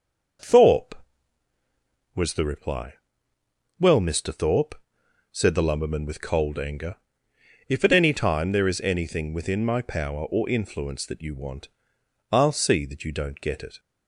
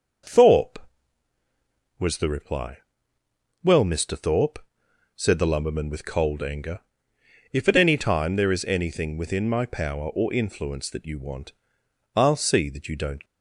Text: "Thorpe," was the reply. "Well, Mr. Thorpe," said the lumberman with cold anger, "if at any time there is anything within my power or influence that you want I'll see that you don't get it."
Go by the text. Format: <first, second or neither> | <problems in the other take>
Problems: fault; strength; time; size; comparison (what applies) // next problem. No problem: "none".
first | pauses between "want" and "I'll"; noticeable; at 11.5 s; 0.64 s long; noticeable in the first // stops before "get it"; at 13.2 s